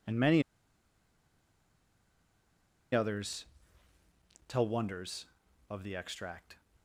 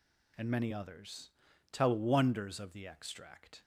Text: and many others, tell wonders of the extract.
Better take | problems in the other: second | pauses between "many" and "others"; strong; at 0.4 s; 2.5 s long

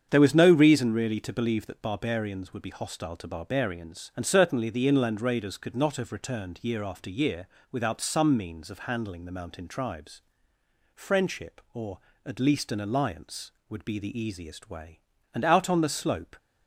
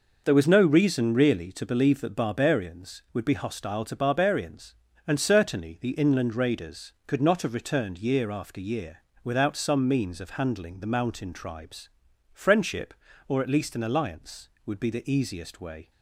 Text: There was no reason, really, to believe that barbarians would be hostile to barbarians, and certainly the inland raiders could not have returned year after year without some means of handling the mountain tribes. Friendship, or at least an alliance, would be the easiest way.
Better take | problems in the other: second | starts louder than the rest; strong; until 1.1 s; 7.5 dB // pauses between "year" and "without"; slight; at 7.4 s; 0.24 s long; slight in the second // goes on to say "And out on the slope"; noticeable; from 15.3 s on; 1.0 s long

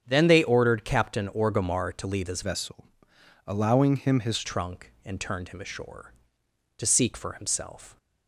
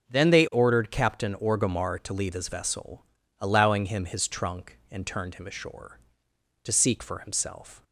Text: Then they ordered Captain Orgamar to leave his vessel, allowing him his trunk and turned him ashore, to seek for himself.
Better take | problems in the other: second | starts louder than the rest; strong; until 1.0 s; 7.5 dB; noticeable in the second // changes voice from "vessel" to "his"; from 2.4 to 4.4 s; 2.0 s long

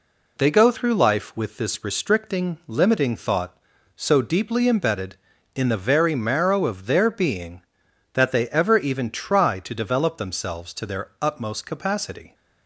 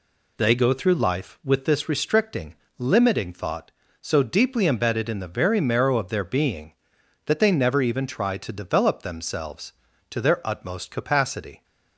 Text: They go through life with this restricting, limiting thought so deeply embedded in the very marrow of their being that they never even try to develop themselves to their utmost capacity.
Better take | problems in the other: second | says "ever" for "never"; at 8.4 s

